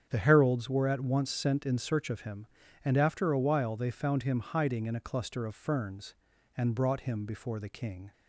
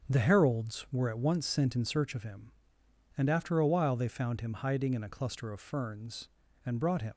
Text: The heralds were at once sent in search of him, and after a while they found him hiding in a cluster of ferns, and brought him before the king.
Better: first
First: starts louder than the rest; strong; until 1.1 s; 8 dB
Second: starts louder than the rest; until 1.1 s; 7 dB // stops before "before the king"; at 7.1 s

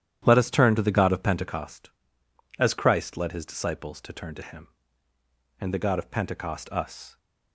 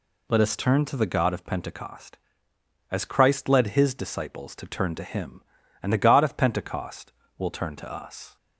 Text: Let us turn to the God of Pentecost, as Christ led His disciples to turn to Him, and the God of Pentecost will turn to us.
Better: second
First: starts louder than the rest; strong; until 1.2 s; 11 dB // skips "will turn to"; at 6.6 s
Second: none

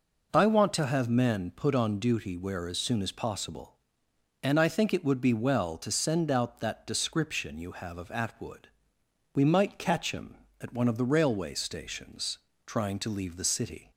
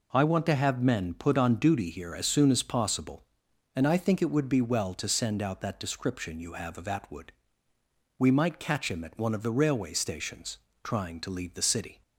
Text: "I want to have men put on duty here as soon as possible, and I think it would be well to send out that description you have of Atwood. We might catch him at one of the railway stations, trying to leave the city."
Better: second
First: says "where" for "here"; at 2.3 s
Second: none

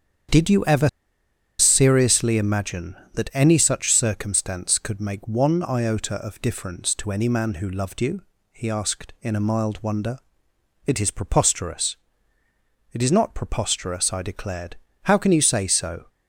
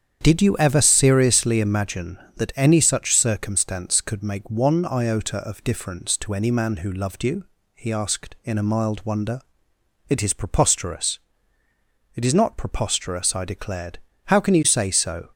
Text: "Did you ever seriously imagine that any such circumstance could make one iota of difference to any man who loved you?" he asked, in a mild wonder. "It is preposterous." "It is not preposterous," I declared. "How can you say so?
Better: second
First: starts louder than the rest; strong; until 2.0 s; 8.5 dB // pauses between "ever" and "seriously"; noticeable; at 0.8 s; 0.71 s long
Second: starts louder than the rest; strong; until 1.2 s; 8.5 dB

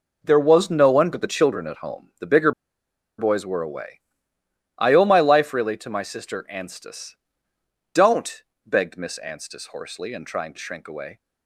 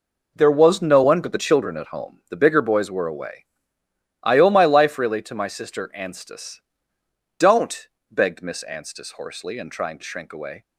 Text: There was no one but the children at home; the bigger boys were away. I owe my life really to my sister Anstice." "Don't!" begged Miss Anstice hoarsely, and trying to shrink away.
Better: second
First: pauses between "bigger" and "boys"; noticeable; at 2.5 s; 0.66 s long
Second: none

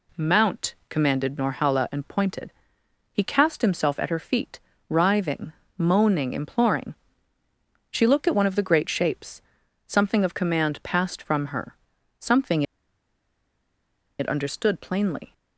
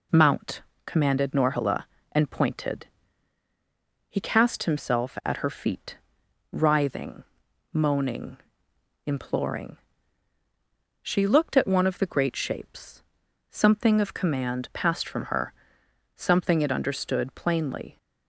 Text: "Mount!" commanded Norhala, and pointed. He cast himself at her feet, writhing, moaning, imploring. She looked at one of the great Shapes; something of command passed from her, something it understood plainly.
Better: second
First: pauses between "something" and "it"; strong; at 12.6 s; 1.5 s long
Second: none

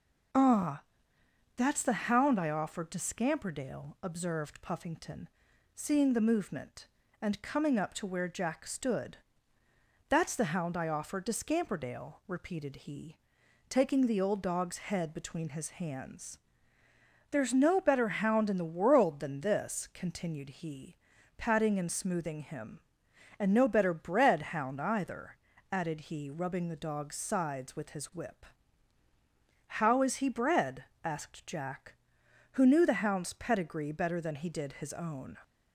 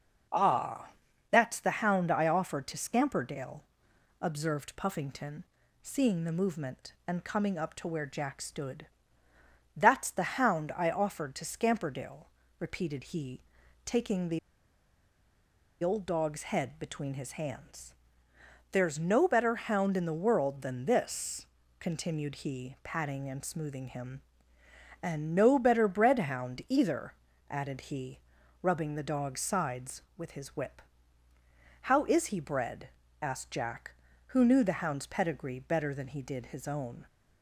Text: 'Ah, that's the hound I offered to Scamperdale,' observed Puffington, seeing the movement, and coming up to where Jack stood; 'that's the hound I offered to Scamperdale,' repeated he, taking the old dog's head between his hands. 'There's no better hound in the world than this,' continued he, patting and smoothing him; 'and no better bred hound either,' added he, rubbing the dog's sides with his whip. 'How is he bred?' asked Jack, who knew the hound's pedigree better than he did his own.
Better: first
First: none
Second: pauses between "the" and "old"; strong; at 14.3 s; 1.4 s long

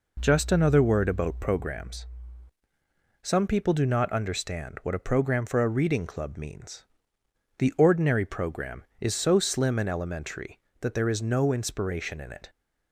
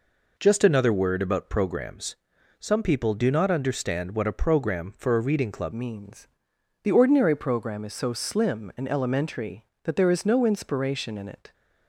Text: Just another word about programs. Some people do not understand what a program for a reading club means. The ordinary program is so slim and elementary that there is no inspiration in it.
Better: first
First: none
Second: changes voice at "means"; from 5.7 s on; 5.8 s long

